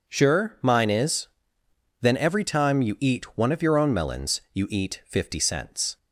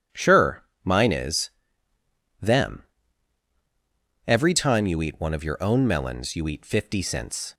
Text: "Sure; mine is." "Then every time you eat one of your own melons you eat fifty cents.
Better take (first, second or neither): first